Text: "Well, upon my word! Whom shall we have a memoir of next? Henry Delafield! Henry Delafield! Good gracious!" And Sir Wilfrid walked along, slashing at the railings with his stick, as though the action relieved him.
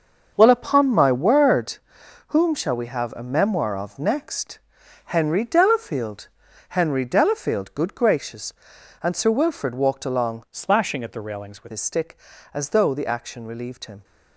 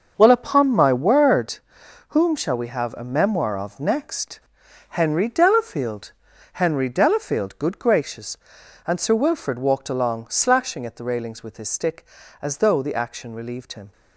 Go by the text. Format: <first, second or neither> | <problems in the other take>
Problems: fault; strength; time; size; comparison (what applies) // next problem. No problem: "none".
second | starts louder than the rest; until 1.3 s; 6 dB; also in the second // changes voice from "slashing" to "with"; from 10.5 to 11.7 s; 1.2 s long